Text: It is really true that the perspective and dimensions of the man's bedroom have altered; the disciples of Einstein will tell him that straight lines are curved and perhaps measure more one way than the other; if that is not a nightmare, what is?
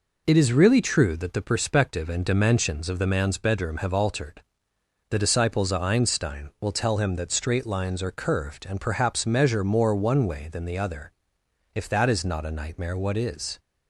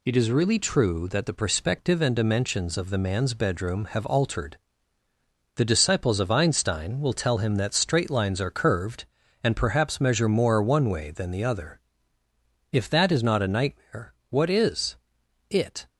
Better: first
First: none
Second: goes on to say "It"; slight; from 15.5 s on; 0.38 s long

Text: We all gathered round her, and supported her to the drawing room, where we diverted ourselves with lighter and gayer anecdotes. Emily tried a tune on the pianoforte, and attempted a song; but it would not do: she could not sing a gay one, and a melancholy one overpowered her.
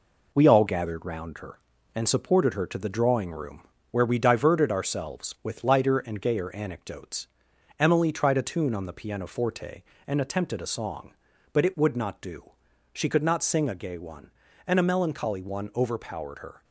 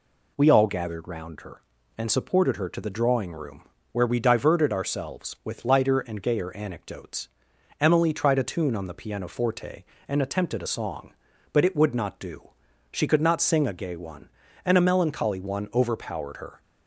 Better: second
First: gets quieter; noticeable; throughout; 4.5 dB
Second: none

